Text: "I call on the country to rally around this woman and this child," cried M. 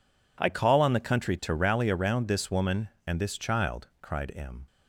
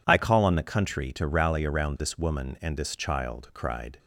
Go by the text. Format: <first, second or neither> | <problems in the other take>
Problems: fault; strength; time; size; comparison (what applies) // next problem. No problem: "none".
first | stops before "M"; at 3.9 s